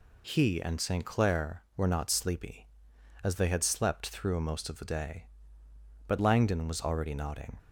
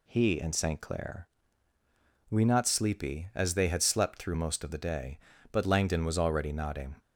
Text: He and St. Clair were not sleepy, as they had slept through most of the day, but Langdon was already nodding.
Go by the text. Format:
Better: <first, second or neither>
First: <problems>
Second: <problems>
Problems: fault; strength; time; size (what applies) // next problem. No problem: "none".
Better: first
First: none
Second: says "we" for "were"; at 2.2 s